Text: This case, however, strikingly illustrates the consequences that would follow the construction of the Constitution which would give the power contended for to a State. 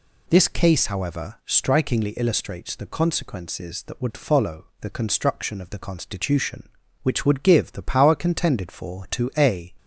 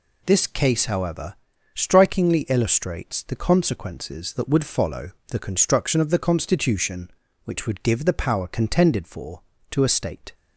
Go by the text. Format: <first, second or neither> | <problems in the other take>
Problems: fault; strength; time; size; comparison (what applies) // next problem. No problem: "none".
second | pauses between "follow" and "the"; slight; at 4.6 s; 0.16 s long; slight in the second // stops before "State"; at 9.7 s